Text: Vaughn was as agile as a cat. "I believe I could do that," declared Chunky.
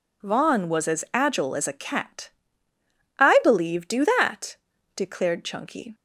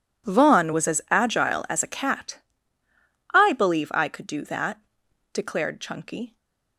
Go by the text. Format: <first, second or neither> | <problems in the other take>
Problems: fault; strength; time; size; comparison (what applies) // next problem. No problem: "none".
second | skips "I could"; at 3.8 s